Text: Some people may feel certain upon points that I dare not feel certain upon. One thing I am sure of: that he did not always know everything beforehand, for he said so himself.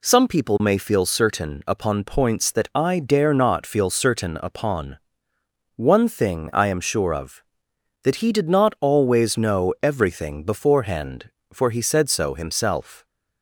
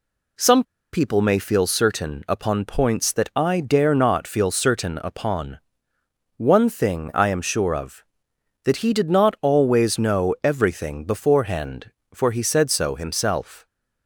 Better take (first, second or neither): first